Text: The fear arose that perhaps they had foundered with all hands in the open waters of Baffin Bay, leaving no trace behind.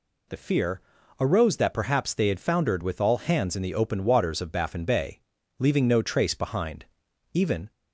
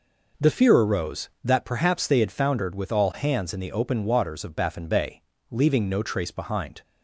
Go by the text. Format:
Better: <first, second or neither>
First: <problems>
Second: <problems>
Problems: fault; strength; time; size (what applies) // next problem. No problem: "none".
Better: second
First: pauses between "fear" and "arose"; slight; at 0.8 s; 0.36 s long // goes on to say "Even"; slight; from 7.3 s on; 0.38 s long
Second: none